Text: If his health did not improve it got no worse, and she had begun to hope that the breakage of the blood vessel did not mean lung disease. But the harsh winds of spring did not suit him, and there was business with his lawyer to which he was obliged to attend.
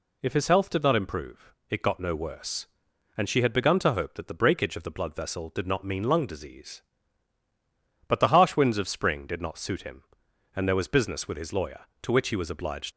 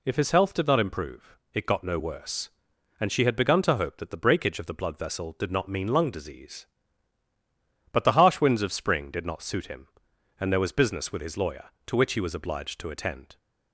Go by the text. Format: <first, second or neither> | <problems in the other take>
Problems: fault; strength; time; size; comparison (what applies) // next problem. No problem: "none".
second | pauses between "improve" and "it"; slight; at 1.5 s; 0.20 s long; slight in the second // stops before "to attend"; at 12.9 s